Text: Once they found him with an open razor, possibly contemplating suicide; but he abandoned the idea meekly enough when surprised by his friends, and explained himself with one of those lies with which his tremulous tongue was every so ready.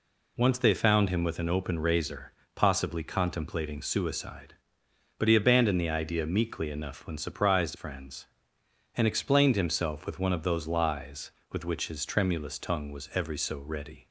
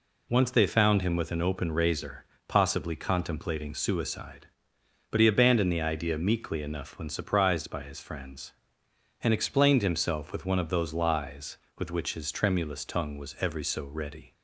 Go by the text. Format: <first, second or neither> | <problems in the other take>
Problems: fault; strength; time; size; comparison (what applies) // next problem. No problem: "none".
second | skips "by his"; at 7.7 s